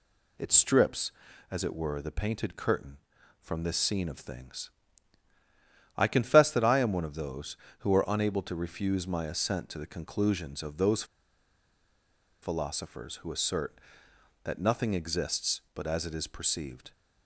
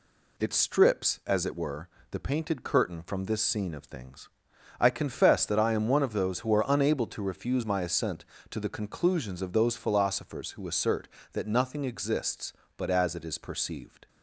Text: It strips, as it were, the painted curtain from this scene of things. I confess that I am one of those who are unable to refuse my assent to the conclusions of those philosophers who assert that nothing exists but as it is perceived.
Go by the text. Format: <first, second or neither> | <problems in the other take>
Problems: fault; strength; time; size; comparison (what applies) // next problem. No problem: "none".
second | pauses between "those" and "philosophers"; strong; at 11.0 s; 1.3 s long